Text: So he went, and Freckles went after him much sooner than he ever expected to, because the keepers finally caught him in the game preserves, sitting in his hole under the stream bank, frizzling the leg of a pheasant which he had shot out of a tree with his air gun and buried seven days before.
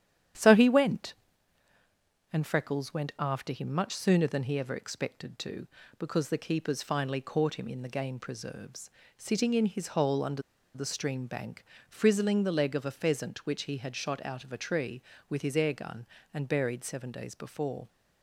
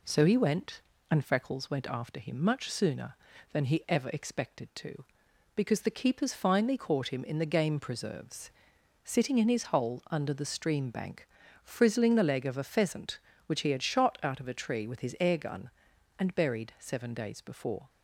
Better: second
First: starts louder than the rest; strong; until 2.5 s; 10 dB // pauses between "under" and "the"; slight; at 10.4 s; 0.32 s long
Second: none

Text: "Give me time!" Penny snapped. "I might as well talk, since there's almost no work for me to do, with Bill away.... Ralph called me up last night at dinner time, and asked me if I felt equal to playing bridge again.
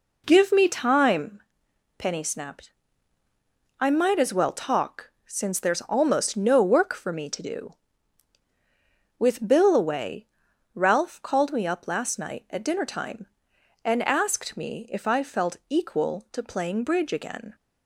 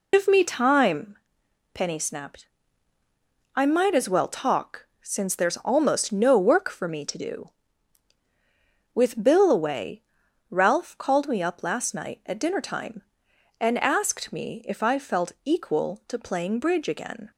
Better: first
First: none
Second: loses the start of "Give"; at 0.1 s; 130 ms

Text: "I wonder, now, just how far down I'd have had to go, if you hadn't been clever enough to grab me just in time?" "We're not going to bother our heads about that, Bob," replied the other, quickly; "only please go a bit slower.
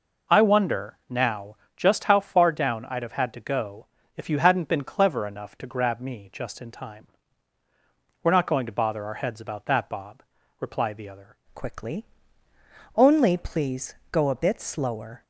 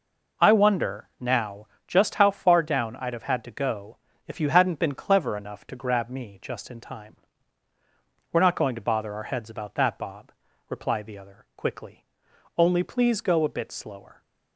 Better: second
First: changes voice at "quickly"; from 11.5 s on; 3.7 s long // pauses between "please" and "go"; slight; at 13.9 s; 0.18 s long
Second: none

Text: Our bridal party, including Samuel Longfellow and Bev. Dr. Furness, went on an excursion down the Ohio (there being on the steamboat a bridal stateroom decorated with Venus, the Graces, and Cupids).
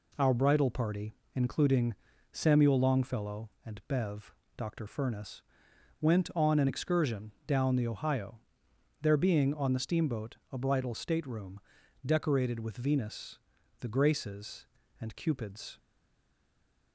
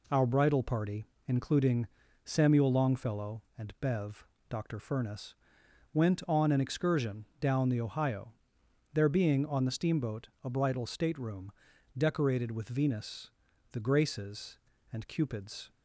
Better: second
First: pauses between "including" and "Samuel"; slight; at 1.9 s; 0.36 s long // pauses between "steamboat" and "a"; slight; at 10.3 s; 0.16 s long // pauses between "stateroom" and "decorated"; noticeable; at 11.5 s; 0.46 s long // stays silent after the last word; noticeable; from 15.7 s on; 1.2 s long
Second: pauses between "including" and "Samuel"; slight; at 1.8 s; 0.36 s long // pauses between "steamboat" and "a"; slight; at 10.2 s; 0.16 s long // pauses between "stateroom" and "decorated"; noticeable; at 11.4 s; 0.46 s long

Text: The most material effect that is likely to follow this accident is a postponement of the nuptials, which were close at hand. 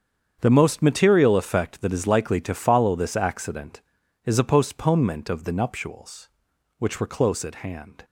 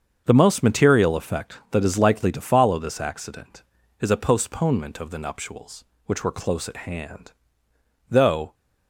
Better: first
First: starts louder than the rest; strong; until 1.4 s; 8 dB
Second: starts louder than the rest; until 1.2 s; 7 dB // goes on to say "Though"; slight; from 8.0 s on; 0.46 s long

